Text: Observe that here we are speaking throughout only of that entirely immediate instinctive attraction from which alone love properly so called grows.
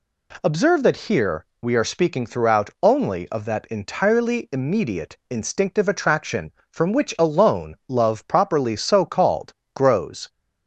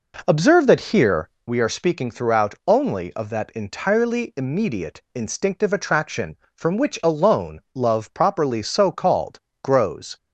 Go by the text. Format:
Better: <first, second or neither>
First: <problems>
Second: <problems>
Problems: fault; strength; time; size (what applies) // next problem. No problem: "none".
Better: first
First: pauses between "here" and "we"; slight; at 1.4 s; 0.18 s long // pauses between "called" and "grows"; slight; at 9.5 s; 0.22 s long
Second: starts louder than the rest; noticeable; until 1.5 s; 4 dB // pauses between "here" and "we"; slight; at 1.2 s; 0.18 s long // pauses between "alone" and "love"; slight; at 7.5 s; 0.15 s long // pauses between "called" and "grows"; slight; at 9.3 s; 0.24 s long